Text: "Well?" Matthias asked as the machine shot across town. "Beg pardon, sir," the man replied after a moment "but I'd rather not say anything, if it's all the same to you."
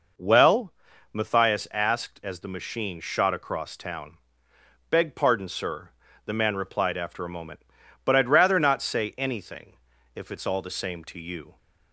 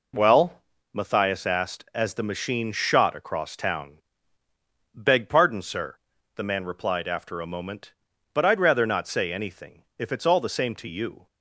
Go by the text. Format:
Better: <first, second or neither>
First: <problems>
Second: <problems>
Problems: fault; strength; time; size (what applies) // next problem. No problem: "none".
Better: neither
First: none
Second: none